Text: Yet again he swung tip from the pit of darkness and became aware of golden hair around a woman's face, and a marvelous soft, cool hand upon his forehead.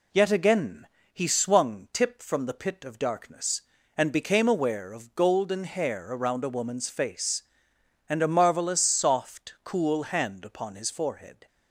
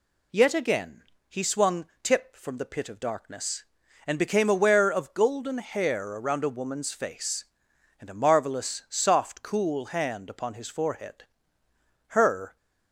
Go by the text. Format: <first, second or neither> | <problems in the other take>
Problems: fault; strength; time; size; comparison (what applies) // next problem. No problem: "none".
first | pauses between "again" and "he"; slight; at 1.0 s; 0.26 s long; slight in the first // pauses between "swung" and "tip"; slight; at 1.8 s; 0.16 s long // goes on to say "Her"; slight; from 12.0 s on; 0.48 s long